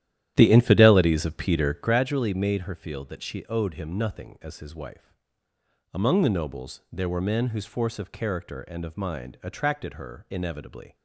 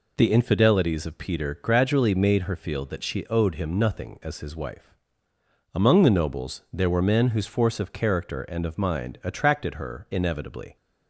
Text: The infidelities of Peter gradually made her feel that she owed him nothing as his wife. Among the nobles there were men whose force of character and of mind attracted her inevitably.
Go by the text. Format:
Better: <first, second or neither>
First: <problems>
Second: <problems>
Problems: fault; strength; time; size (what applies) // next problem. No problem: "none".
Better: second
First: starts louder than the rest; strong; until 2.1 s; 12 dB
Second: none